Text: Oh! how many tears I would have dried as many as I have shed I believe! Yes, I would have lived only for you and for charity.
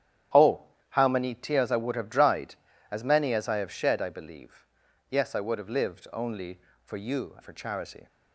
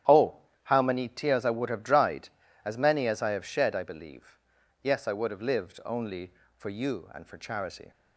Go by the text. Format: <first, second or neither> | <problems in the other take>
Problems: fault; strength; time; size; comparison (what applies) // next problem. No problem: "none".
second | starts louder than the rest; strong; until 1.6 s; 11 dB; strong in the second // skips "and"; at 7.3 s